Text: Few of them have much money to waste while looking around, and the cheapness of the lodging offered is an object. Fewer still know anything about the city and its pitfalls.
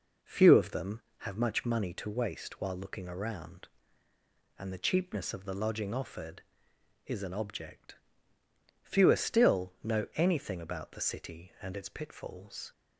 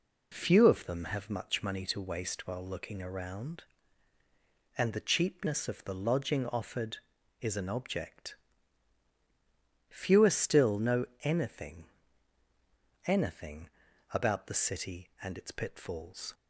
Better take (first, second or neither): first